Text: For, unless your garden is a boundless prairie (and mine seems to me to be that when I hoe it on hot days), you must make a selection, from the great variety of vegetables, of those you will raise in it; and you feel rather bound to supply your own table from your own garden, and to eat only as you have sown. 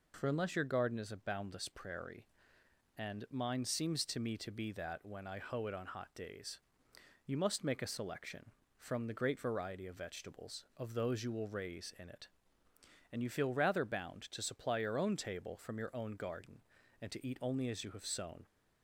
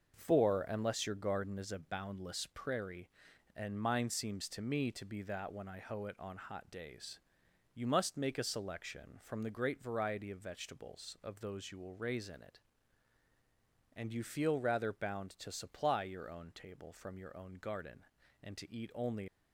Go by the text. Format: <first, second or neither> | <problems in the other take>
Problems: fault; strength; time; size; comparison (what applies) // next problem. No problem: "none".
first | starts louder than the rest; until 1.1 s; 6.5 dB // stops before "as you have sown"; at 19.2 s